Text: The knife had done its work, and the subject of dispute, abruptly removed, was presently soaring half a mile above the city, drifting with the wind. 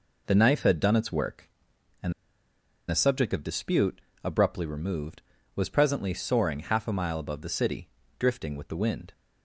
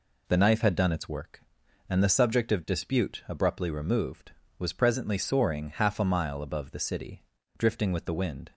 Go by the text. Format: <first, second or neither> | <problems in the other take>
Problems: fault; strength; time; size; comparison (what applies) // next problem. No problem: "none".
second | pauses between "and" and "the"; noticeable; at 2.1 s; 0.76 s long